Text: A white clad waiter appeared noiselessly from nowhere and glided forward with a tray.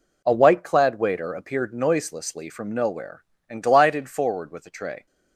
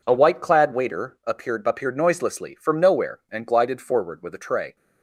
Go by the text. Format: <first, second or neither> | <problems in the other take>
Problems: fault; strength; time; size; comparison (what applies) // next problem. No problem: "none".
first | says "appeared" twice; at 1.6 s